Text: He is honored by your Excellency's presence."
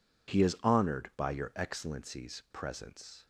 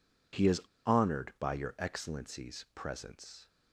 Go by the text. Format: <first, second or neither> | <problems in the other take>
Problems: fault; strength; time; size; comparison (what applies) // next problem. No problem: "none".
first | pauses between "is" and "honored"; slight; at 0.5 s; 0.25 s long